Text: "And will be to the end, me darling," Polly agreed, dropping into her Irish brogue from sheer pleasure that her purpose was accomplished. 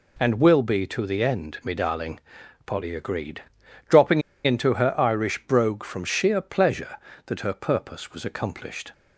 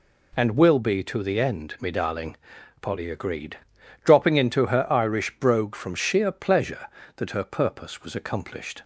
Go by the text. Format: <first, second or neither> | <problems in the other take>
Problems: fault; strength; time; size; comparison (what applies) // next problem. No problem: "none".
second | pauses between "dropping" and "into"; slight; at 4.2 s; 0.23 s long